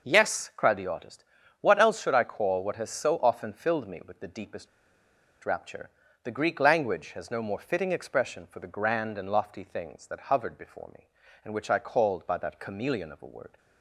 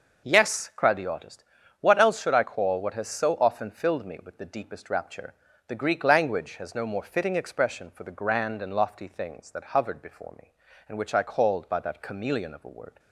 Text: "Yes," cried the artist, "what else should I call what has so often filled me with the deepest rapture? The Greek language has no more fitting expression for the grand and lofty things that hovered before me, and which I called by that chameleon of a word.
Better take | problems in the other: second | pauses between "deepest" and "rapture"; noticeable; at 4.6 s; 0.76 s long

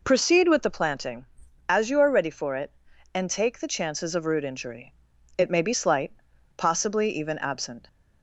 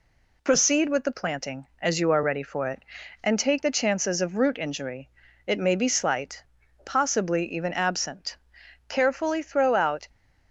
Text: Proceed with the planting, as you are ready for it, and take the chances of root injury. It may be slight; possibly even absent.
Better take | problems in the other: first | goes on to say "Carefully throw out"; noticeable; from 8.8 s on; 1.2 s long

